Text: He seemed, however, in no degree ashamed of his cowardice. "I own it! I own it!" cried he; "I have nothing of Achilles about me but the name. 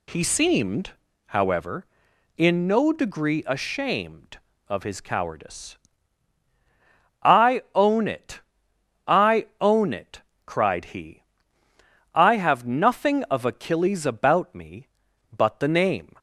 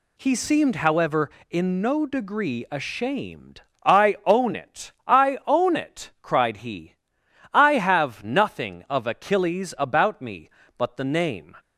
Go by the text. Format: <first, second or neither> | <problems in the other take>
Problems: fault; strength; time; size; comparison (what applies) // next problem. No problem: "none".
first | skips "of his cowardice"; at 3.7 s